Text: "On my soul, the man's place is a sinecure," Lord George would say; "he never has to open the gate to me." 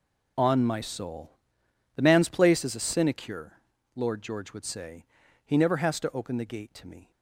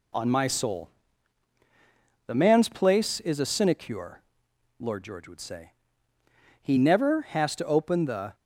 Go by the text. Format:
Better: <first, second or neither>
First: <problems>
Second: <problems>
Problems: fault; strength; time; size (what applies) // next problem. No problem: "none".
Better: first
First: none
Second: stops before "gate to me"; at 8.3 s